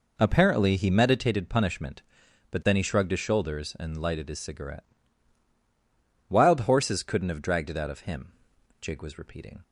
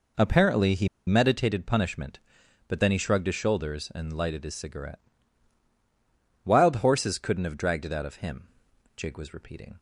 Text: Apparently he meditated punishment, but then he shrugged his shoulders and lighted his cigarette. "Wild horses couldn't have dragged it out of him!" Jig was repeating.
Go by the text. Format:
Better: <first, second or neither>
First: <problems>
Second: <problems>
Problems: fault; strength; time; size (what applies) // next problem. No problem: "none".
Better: first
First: none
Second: pauses between "he" and "meditated"; slight; at 0.8 s; 0.20 s long